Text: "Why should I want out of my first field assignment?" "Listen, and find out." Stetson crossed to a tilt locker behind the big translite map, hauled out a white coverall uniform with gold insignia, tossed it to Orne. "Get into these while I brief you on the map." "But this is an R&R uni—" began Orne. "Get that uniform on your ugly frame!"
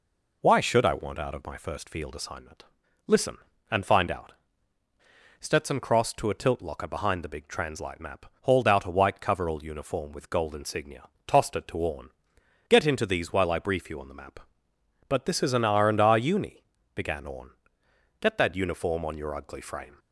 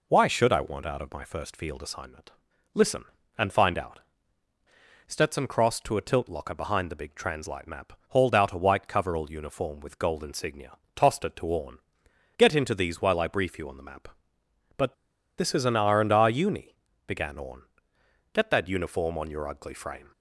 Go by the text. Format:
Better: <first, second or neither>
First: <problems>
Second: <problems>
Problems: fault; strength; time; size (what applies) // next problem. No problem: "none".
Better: first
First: none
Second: pauses between "But" and "this"; at 14.9 s; 0.43 s long